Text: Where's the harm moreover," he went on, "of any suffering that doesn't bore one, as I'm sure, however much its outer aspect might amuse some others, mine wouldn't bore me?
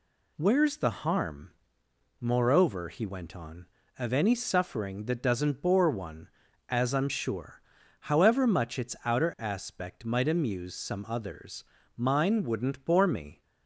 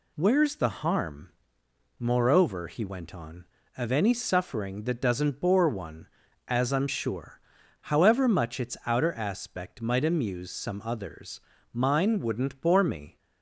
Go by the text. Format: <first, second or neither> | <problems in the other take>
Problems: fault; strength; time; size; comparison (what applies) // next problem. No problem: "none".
neither | pauses between "harm" and "moreover"; noticeable; the same in both